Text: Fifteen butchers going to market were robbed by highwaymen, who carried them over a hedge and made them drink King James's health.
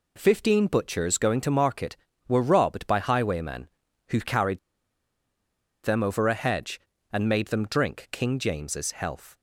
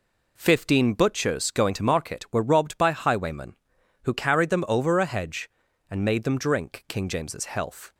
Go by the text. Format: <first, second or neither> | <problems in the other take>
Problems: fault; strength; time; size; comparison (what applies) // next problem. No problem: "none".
second | pauses between "carried" and "them"; strong; at 4.5 s; 1.2 s long